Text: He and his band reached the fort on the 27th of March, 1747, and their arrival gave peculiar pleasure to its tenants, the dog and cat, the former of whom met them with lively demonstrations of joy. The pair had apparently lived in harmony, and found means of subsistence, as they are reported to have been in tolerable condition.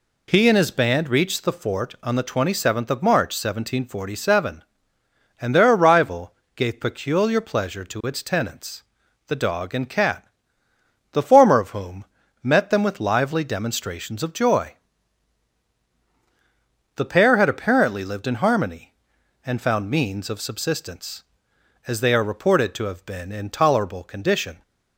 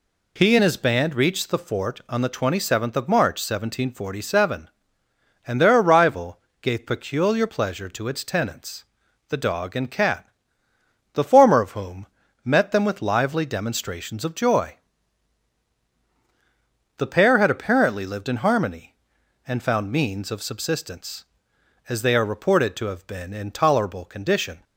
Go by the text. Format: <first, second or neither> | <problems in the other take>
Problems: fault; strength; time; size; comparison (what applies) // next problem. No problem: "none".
neither | pauses between "arrival" and "gave"; slight; the same in both // pauses between "whom" and "met"; slight; the same in both